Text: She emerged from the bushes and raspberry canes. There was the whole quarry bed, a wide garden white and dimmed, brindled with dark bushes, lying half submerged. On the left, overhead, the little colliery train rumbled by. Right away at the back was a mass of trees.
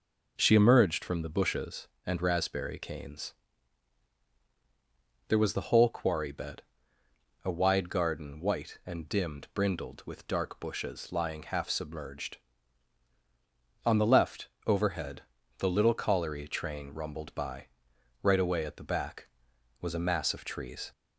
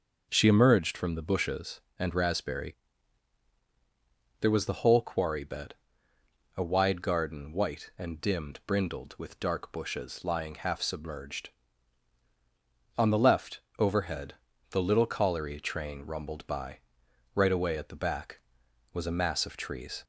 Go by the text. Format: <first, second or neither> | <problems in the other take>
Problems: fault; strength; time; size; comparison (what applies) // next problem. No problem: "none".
first | starts louder than the rest; noticeable; until 1.3 s; 6 dB // skips "canes"; at 3.5 s